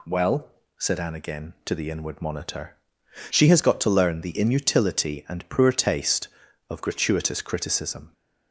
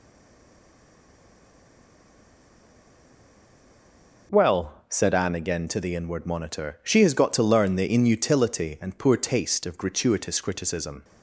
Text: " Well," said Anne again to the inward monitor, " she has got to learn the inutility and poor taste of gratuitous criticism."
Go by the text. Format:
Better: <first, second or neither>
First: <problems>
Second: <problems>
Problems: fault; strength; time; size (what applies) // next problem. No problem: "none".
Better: first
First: none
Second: stays silent before the first word; strong; until 4.2 s; 4.2 s long